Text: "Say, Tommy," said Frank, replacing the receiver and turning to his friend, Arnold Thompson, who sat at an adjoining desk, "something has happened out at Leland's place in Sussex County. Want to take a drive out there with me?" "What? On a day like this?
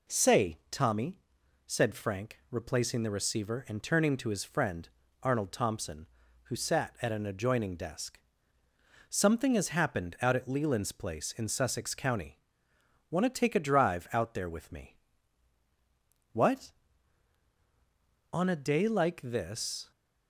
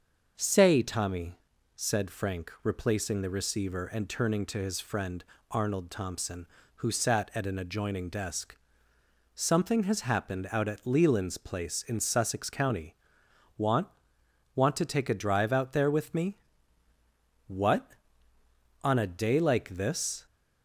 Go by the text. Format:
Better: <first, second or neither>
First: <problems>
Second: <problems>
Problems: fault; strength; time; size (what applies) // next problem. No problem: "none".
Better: first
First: none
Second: starts louder than the rest; noticeable; until 1.3 s; 6 dB // says "Want" twice; at 14.5 s